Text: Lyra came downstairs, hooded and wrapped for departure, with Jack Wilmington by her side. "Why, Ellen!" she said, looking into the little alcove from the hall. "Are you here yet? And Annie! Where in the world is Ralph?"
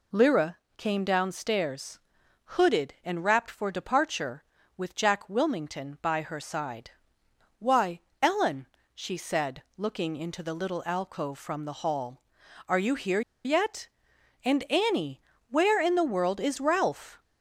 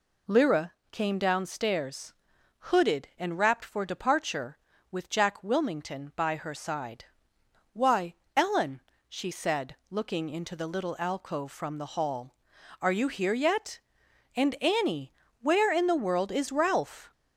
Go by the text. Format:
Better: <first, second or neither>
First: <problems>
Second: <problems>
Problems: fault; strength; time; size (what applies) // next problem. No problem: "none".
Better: second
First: pauses between "Lyra" and "came"; slight; at 0.5 s; 0.20 s long // pauses between "here" and "yet"; slight; at 13.2 s; 0.24 s long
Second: pauses between "Lyra" and "came"; slight; at 0.7 s; 0.18 s long